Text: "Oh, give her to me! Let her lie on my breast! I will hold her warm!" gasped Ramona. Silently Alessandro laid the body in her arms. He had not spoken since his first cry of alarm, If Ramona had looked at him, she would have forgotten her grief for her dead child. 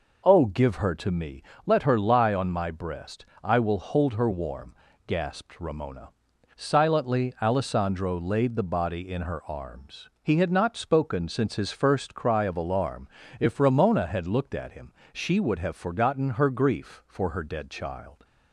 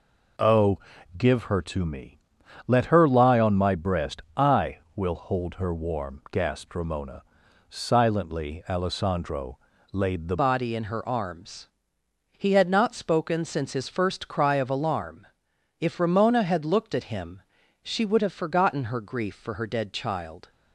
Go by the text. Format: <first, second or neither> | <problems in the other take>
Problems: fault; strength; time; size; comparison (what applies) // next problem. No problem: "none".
first | pauses between "Alessandro" and "laid"; slight; at 9.5 s; 0.36 s long // changes voice at "body"; from 10.3 s on; 10.2 s long